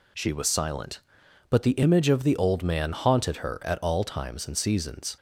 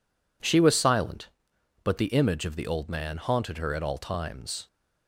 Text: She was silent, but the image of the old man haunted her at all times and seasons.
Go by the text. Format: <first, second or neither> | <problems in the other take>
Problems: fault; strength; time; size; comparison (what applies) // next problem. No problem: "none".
first | stops before "and seasons"; at 4.6 s